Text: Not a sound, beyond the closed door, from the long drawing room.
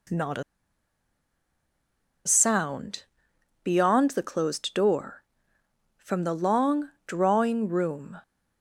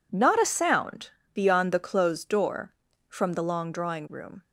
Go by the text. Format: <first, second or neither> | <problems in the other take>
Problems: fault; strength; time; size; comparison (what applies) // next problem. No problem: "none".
second | pauses between "a" and "sound"; strong; at 0.4 s; 1.8 s long // pauses between "long" and "drawing"; slight; at 6.9 s; 0.18 s long